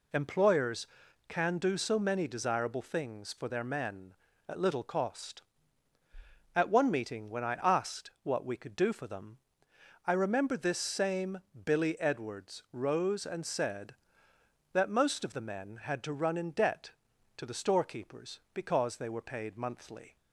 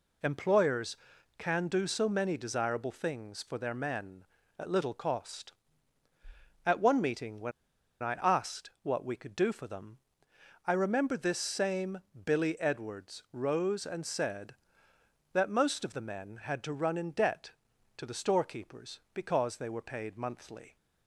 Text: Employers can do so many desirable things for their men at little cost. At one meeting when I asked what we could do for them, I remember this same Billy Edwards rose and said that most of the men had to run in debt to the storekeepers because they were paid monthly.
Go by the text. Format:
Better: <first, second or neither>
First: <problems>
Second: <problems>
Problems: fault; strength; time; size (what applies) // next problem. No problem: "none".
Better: first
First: pauses between "same" and "Billy"; slight; at 11.3 s; 0.26 s long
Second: pauses between "when" and "I"; noticeable; at 7.5 s; 0.50 s long // pauses between "same" and "Billy"; slight; at 11.9 s; 0.26 s long